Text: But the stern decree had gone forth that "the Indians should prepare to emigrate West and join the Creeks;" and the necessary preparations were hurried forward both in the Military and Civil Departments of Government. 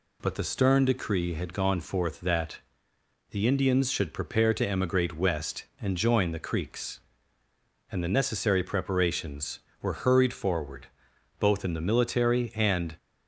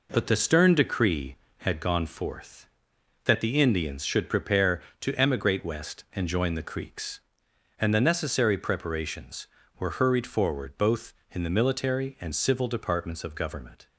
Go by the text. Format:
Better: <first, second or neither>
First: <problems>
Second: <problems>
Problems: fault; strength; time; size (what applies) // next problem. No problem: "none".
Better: second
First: pauses between "that" and "the"; noticeable; at 2.5 s; 0.72 s long // pauses between "forward" and "both"; noticeable; at 10.8 s; 0.54 s long // stops before "Civil Departments of Government"; at 12.9 s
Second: none